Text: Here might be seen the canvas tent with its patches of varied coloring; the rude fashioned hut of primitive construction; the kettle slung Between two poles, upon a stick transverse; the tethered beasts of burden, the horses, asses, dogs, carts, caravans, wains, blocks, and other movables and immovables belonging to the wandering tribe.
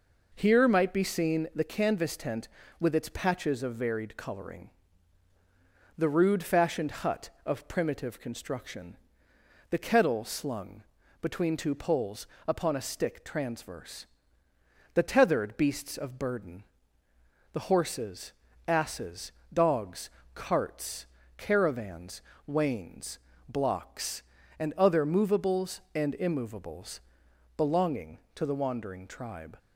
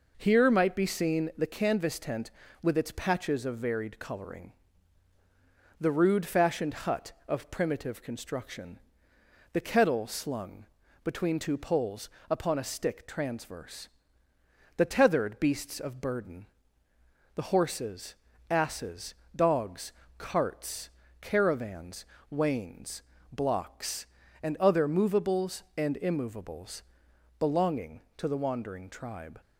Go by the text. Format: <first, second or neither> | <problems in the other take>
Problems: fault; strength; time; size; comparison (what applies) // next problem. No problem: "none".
neither | pauses between "slung" and "Between"; the same in both // pauses between "immovables" and "belonging"; noticeable; the same in both